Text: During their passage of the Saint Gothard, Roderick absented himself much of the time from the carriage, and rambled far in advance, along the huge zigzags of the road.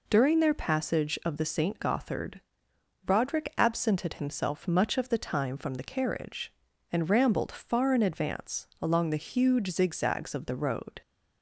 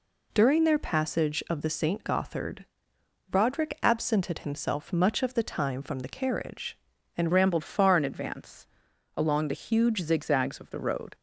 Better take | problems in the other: first | changes voice at "rambled"; from 7.3 s on; 3.8 s long

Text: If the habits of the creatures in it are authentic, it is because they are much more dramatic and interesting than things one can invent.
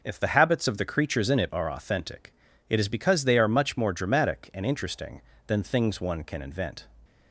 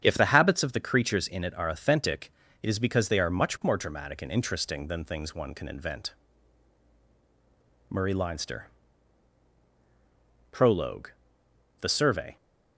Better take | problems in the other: first | starts louder than the rest; strong; until 1.0 s; 8 dB // goes on to say "Murray Leinster PROLOGUE The Survey"; strong; from 7.9 s on; 4.4 s long

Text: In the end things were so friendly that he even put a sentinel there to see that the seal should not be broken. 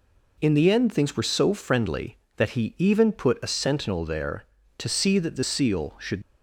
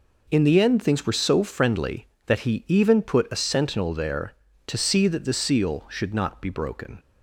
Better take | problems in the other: second | stops before "not be broken"; at 6.2 s

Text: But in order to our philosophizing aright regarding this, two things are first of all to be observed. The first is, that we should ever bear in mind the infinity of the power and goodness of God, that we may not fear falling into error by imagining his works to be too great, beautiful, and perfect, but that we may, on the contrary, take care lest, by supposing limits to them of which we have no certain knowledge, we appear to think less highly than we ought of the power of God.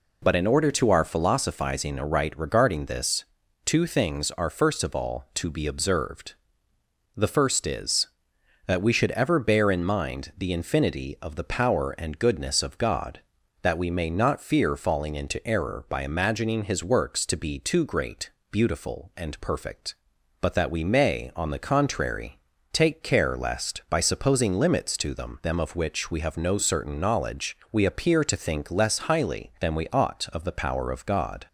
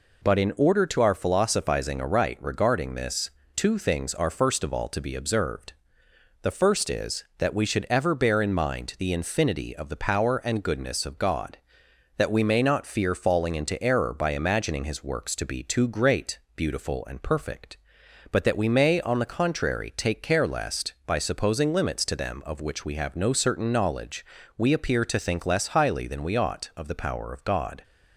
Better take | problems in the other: second | says "them" twice; at 25.4 s

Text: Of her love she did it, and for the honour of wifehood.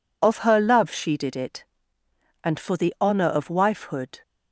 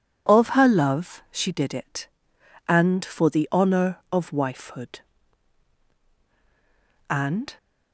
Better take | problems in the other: first | goes on to say "And"; slight; from 7.0 s on; 0.48 s long

